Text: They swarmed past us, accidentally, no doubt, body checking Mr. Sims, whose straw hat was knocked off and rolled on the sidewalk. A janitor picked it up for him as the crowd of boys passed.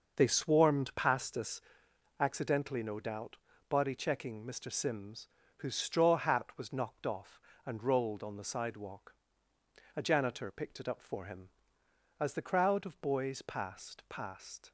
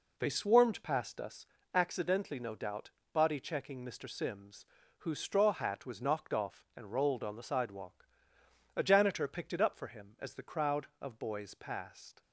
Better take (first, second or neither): second